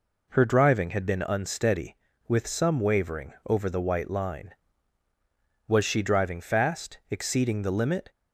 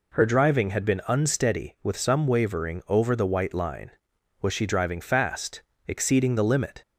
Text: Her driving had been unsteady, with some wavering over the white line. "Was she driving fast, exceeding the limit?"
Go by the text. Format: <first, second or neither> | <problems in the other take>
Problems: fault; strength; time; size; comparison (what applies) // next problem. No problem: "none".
neither | none